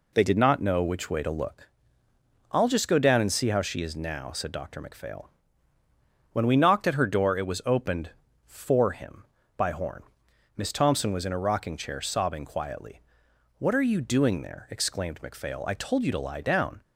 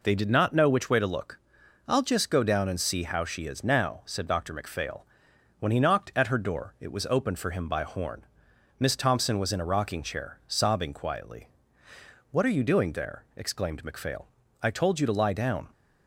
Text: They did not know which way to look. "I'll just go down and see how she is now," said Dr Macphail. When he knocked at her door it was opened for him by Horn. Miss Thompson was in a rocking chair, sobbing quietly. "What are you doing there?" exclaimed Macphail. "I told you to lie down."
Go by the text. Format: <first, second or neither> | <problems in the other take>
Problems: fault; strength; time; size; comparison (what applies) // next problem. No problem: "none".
second | says "we" for "he"; at 6.4 s